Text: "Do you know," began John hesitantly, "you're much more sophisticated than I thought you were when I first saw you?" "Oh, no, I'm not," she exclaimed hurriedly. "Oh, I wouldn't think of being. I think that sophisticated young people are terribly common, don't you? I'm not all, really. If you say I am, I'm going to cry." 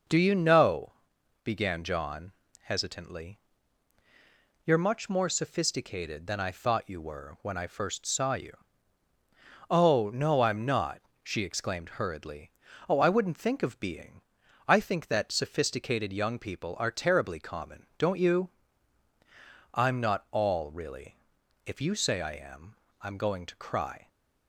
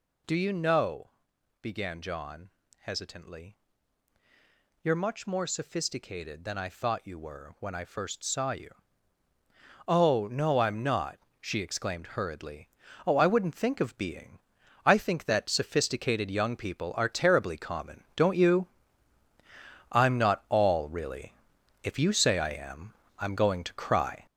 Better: first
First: pauses between "John" and "hesitantly"; slight; at 2.3 s; 0.30 s long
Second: gets louder; throughout; 6.5 dB // pauses between "John" and "hesitantly"; slight; at 2.4 s; 0.30 s long

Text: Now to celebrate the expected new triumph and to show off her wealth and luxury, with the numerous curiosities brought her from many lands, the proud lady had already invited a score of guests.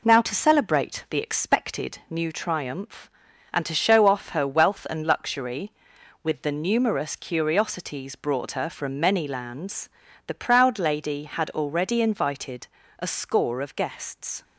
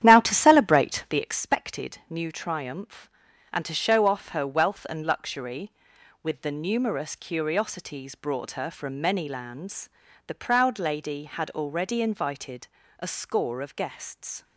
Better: first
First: pauses between "invited" and "a"; slight; at 12.6 s; 0.32 s long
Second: starts louder than the rest; strong; until 1.3 s; 10.5 dB // pauses between "invited" and "a"; slight; at 12.6 s; 0.32 s long

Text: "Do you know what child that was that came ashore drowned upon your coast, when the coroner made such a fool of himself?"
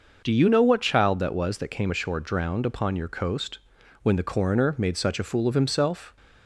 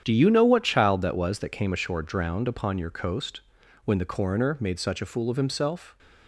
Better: first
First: starts louder than the rest; noticeable; until 1.2 s; 6 dB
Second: gets quieter; strong; throughout; 11.5 dB // starts louder than the rest; strong; until 1.0 s; 9 dB

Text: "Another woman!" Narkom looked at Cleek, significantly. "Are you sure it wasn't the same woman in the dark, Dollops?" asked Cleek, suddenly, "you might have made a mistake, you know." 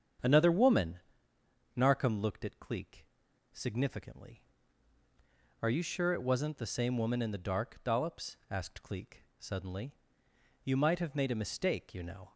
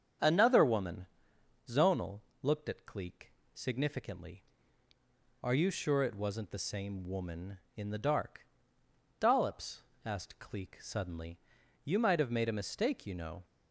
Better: first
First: starts louder than the rest; strong; until 1.9 s; 8 dB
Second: starts louder than the rest; strong; until 1.8 s; 7.5 dB // says "Zonal" for "Narkom"; at 1.6 s

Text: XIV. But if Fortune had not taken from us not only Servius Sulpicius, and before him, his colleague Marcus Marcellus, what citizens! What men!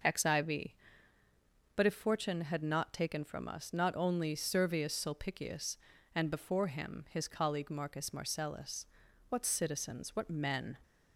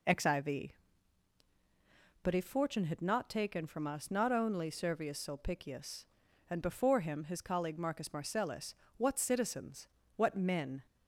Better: neither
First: none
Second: none

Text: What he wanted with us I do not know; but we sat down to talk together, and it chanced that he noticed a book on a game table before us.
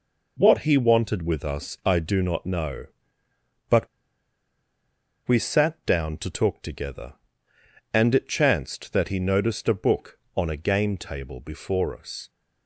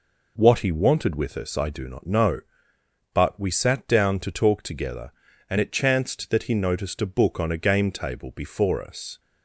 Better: second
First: pauses between "but" and "we"; strong; at 3.8 s; 1.3 s long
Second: none

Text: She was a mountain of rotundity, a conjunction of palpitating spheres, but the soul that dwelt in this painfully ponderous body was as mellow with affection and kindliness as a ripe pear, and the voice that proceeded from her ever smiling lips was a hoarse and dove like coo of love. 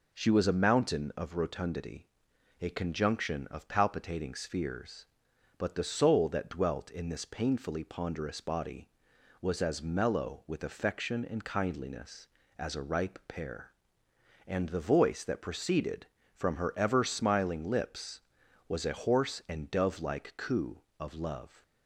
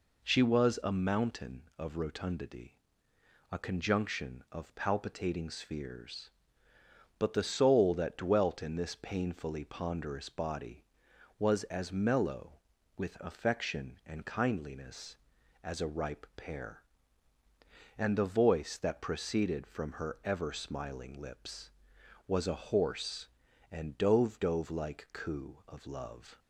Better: first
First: none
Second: says "dove" twice; at 24.3 s

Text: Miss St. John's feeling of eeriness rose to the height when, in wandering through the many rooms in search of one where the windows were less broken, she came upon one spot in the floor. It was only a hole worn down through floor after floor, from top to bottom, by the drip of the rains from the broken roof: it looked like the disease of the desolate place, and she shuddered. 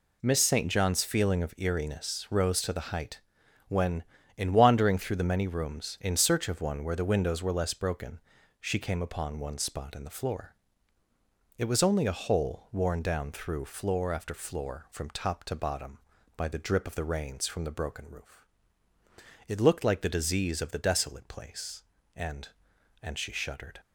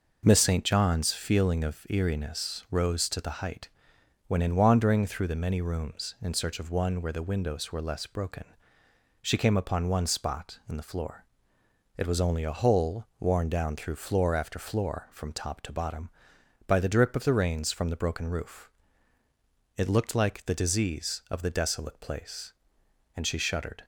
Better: second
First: pauses between "height" and "when"; noticeable; at 3.1 s; 0.48 s long // says "and" twice; at 23.0 s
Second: pauses between "height" and "when"; noticeable; at 3.6 s; 0.58 s long

